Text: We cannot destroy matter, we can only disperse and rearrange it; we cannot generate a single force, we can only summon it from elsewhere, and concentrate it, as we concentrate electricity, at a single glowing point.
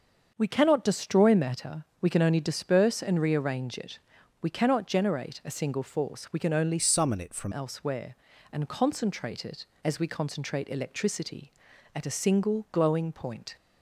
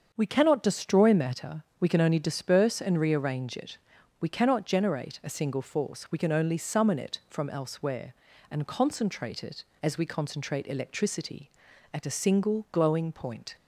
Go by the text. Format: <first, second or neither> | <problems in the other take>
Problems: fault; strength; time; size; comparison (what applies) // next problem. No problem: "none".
second | starts louder than the rest; until 1.3 s; 7 dB; also in the second // changes voice from "summon" to "from"; from 6.7 to 7.5 s; 0.8 s long